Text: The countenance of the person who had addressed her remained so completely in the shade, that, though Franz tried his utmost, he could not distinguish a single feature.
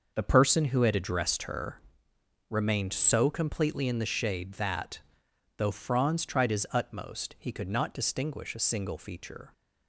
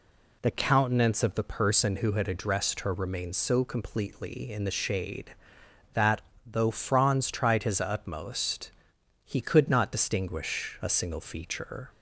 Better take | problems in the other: second | starts louder than the rest; noticeable; until 1.1 s; 6 dB // skips "countenance of the"; at 0.2 s // pauses between "her" and "remained"; noticeable; at 1.8 s; 0.70 s long

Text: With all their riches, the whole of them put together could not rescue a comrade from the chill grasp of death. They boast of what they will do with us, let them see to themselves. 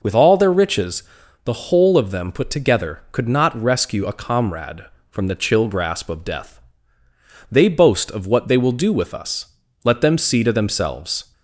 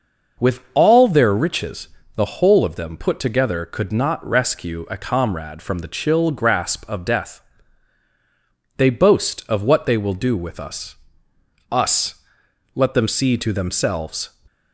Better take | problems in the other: first | says "us" twice; at 11.7 s

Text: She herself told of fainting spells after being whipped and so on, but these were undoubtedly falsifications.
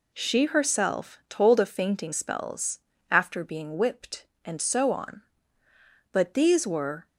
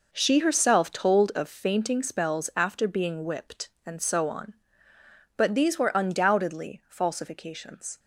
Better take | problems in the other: second | pauses between "spells" and "after"; slight; at 2.7 s; 0.30 s long // stops before "undoubtedly falsifications"; at 7.0 s

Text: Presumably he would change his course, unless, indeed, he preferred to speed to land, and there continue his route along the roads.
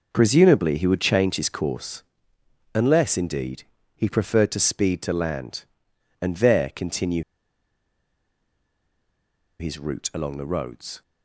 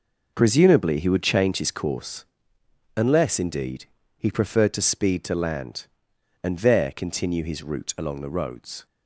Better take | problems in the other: second | pauses between "continue" and "his"; strong; at 7.2 s; 2.3 s long

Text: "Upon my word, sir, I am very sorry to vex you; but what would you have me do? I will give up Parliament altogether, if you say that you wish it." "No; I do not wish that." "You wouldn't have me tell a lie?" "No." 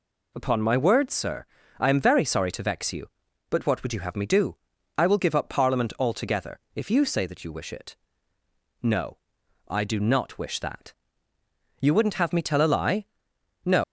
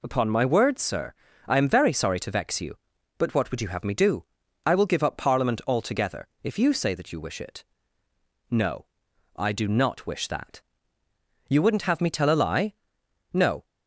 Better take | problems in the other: second | leaves "No" unfinished; at 13.8 s; 130 ms

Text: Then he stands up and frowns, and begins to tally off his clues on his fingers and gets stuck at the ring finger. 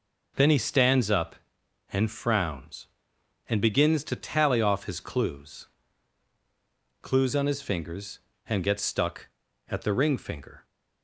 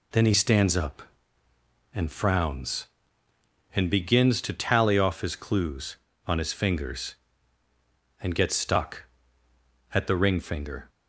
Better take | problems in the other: second | says "clues" twice; at 7.0 s

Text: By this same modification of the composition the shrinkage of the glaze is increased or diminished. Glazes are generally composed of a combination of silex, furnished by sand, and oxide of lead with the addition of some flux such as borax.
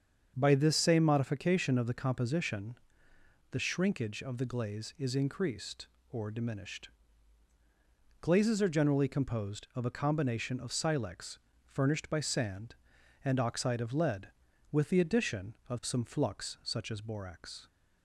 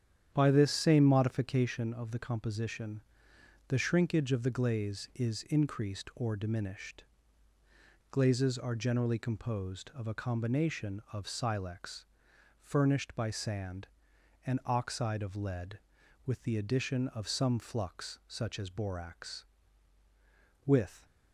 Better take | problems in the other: first | starts louder than the rest; strong; until 1.3 s; 9.5 dB; strong in the first // pauses between "composition" and "the"; noticeable; at 3.0 s; 0.66 s long; noticeable in the first // goes on to say "With"; slight; from 20.6 s on; 0.40 s long

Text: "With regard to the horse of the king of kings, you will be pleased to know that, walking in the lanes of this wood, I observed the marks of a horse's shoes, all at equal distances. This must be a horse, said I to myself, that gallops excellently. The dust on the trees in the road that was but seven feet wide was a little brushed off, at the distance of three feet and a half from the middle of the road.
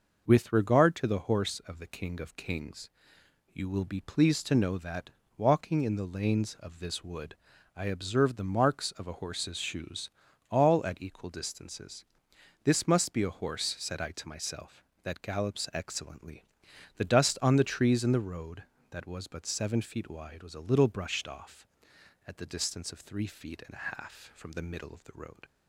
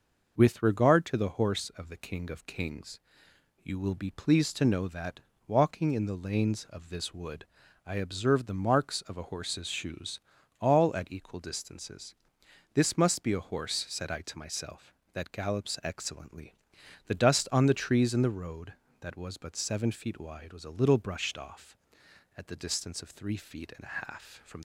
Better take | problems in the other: first | stops before "the middle of the road"; at 24.5 s

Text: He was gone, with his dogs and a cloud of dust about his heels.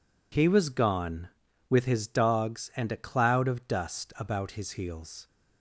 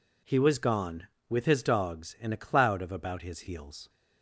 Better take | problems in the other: first | skips "dust"; at 2.9 s

